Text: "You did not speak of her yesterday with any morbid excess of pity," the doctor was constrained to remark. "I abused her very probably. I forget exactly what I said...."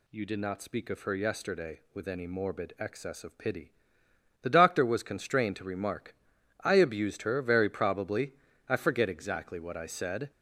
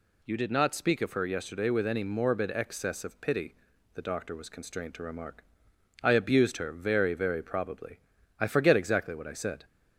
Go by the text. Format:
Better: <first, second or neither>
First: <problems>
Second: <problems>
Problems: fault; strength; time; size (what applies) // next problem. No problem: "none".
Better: first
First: none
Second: says "very" twice; at 7.1 s